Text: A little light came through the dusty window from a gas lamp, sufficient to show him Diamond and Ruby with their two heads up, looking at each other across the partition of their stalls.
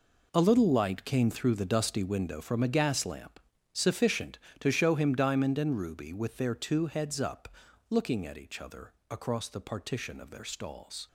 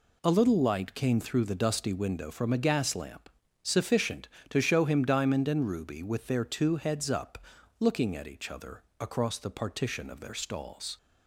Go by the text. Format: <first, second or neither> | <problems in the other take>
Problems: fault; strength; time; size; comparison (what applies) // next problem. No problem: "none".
second | gets quieter; strong; throughout; 12 dB // pauses between "other" and "across"; slight; at 8.9 s; 0.16 s long; slight in the second